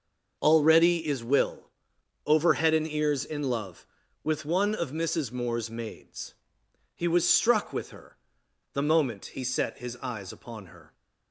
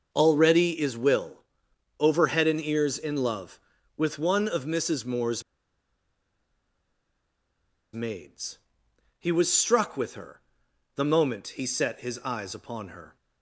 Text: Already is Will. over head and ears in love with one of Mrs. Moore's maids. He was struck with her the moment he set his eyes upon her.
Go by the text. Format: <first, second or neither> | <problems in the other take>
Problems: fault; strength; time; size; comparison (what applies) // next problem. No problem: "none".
first | starts louder than the rest; until 1.1 s; 6 dB; also in the first // pauses between "Moore's" and "maids"; strong; at 5.4 s; 2.5 s long // pauses between "her" and "the"; noticeable; at 10.4 s; 0.52 s long; noticeable in the first